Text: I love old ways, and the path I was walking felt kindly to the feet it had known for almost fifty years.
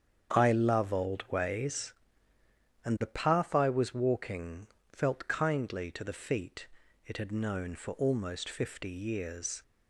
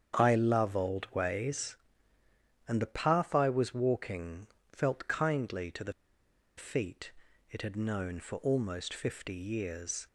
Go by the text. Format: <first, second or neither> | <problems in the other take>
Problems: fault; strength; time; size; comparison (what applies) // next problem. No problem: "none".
first | starts louder than the rest; strong; until 1.2 s; 8 dB; strong in the first // pauses between "walking" and "felt"; slight; at 4.4 s; 0.24 s long; slight in the first // pauses between "the" and "feet"; noticeable; at 5.9 s; 0.64 s long // pauses between "feet" and "it"; at 7.1 s; 0.40 s long; also in the first